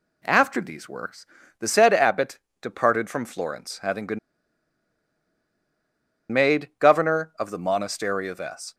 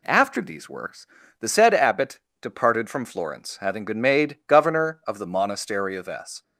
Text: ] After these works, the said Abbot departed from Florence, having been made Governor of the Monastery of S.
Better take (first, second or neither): second